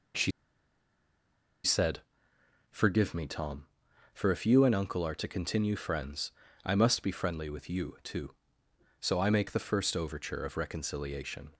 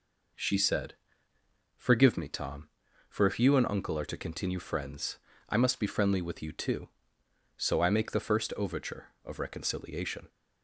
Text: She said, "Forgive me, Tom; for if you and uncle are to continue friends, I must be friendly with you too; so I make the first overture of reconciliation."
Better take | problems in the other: second | pauses between "She" and "said"; strong; at 0.3 s; 1.3 s long

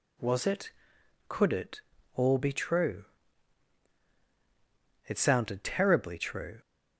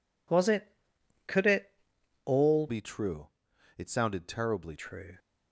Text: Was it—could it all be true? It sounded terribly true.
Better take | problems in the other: first | pauses between "it" and "all"; noticeable; at 1.7 s; 0.54 s long; slight in the first // changes voice from "be" to "terribly"; from 2.6 to 4.7 s; 2.1 s long

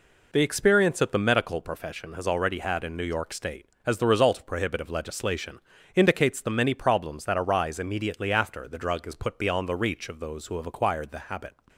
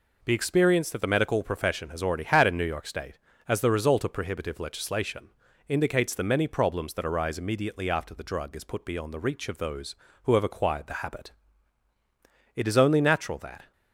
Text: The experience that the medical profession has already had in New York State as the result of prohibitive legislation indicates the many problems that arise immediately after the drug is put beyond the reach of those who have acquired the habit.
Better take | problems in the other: first | pauses between "legislation" and "indicates"; at 5.2 s; 0.38 s long; slight in the first // goes on to say "It is only natural that"; noticeable; from 12.5 s on; 1.1 s long

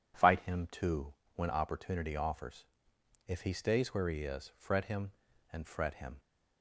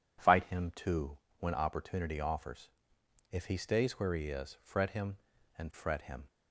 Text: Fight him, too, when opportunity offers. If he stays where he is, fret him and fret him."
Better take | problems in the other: neither | none

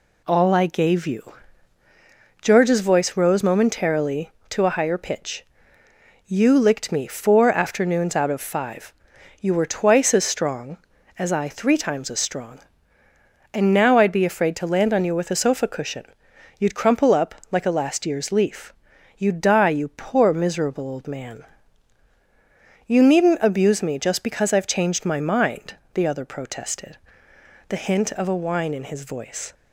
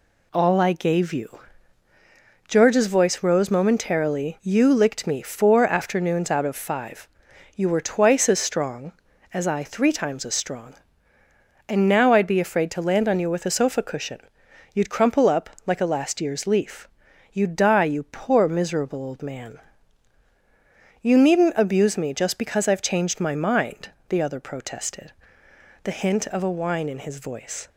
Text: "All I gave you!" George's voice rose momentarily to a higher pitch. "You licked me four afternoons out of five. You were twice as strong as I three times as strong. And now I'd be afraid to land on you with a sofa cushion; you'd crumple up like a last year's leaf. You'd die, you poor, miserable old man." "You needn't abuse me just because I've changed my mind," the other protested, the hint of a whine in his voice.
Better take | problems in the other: first | skips "to a higher pitch"; at 4.3 s // pauses between "up" and "like"; slight; at 15.4 s; 0.16 s long; slight in the first

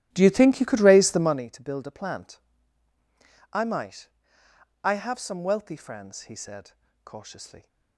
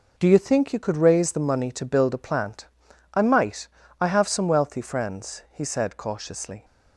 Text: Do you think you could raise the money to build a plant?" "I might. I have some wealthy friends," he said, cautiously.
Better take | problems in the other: second | starts louder than the rest; strong; until 1.4 s; 14 dB

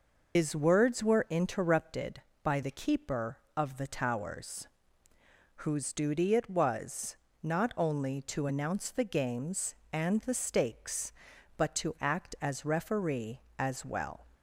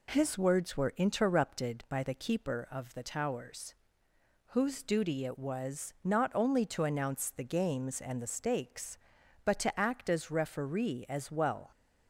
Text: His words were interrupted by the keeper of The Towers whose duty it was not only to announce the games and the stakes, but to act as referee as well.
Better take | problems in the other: second | loses the start of "His"; at 0.3 s; 145 ms // pauses between "Towers" and "whose"; noticeable; at 4.6 s; 0.96 s long; noticeable in the second // pauses between "was" and "not"; slight; at 7.1 s; 0.26 s long

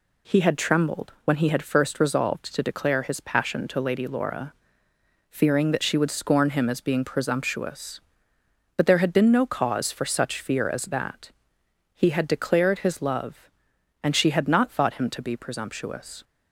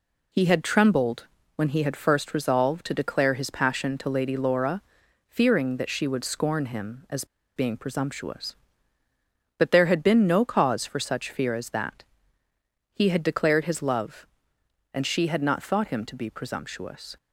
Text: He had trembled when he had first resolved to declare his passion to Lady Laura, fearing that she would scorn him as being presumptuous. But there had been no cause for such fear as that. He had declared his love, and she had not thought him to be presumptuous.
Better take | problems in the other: first | pauses between "trembled" and "when"; slight; at 1.2 s; 0.30 s long // pauses between "as" and "being"; slight; at 7.2 s; 0.30 s long

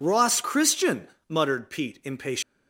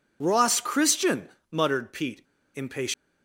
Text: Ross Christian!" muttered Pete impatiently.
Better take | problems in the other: first | pauses between "Pete" and "impatiently"; slight; at 2.2 s; 0.34 s long

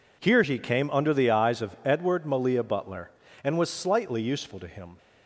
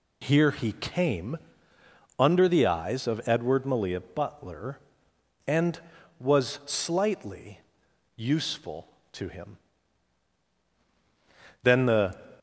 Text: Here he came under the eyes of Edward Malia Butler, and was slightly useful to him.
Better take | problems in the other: first | pauses between "came" and "under"; noticeable; at 1.3 s; 0.80 s long // pauses between "slightly" and "useful"; noticeable; at 7.5 s; 0.56 s long // goes on to say "Then the"; from 11.6 s on; 0.58 s long

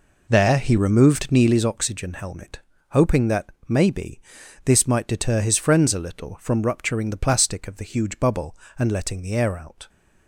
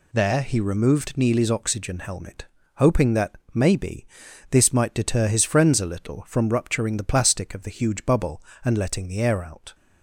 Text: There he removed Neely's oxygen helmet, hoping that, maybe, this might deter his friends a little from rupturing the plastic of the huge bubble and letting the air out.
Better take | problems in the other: second | starts louder than the rest; noticeable; until 1.7 s; 4 dB

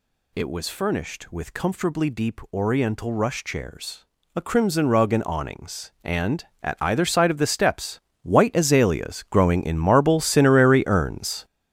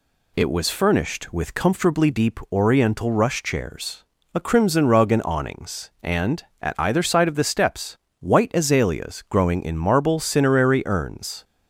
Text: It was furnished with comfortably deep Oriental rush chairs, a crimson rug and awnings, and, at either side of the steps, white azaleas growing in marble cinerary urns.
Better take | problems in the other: second | gets louder; strong; throughout; 10 dB

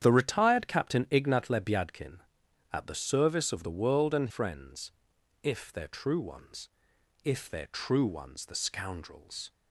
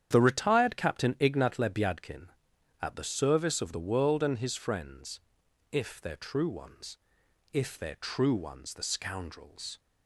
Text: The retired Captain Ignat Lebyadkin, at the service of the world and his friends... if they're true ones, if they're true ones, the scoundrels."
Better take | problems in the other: second | starts louder than the rest; strong; until 1.0 s; 9 dB; strong in the second // skips "his"; at 4.2 s

